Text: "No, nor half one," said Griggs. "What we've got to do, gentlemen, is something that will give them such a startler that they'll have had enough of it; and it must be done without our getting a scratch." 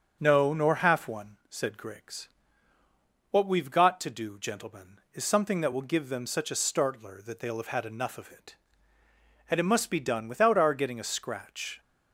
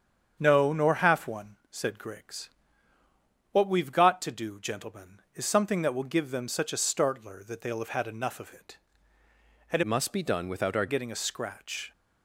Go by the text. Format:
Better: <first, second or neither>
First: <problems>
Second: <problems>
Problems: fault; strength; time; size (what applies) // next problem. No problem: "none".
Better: first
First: starts louder than the rest; until 1.2 s; 7 dB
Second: starts louder than the rest; strong; until 1.4 s; 7.5 dB // changes voice from "must" to "our"; from 9.8 to 10.8 s; 1.0 s long